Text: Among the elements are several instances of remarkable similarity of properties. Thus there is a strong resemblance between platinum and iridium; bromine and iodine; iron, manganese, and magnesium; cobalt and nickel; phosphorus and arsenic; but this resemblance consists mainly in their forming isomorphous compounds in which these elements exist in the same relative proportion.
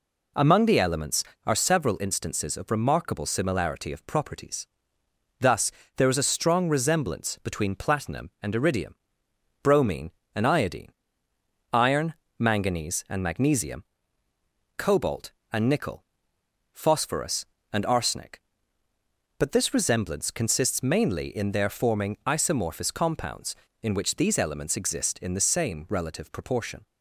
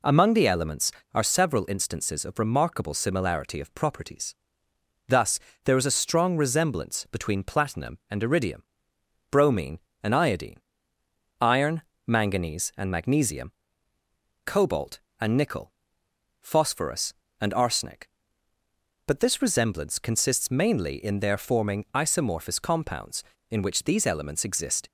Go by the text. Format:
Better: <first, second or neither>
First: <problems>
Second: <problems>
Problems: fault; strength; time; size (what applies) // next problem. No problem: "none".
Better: first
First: pauses between "Thus" and "there"; slight; at 5.7 s; 0.26 s long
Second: pauses between "Thus" and "there"; slight; at 5.3 s; 0.26 s long // stops before "in the same relative proportion"; at 24.8 s